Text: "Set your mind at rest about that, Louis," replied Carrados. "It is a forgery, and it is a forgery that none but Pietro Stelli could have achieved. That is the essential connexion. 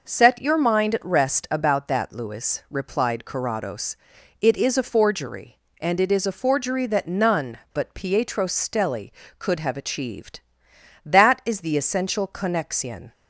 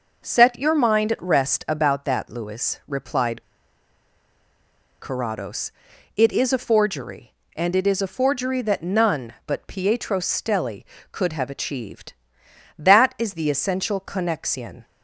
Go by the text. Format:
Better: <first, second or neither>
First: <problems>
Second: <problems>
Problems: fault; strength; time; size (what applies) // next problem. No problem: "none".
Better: first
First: none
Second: pauses between "replied" and "Carrados"; strong; at 3.4 s; 1.5 s long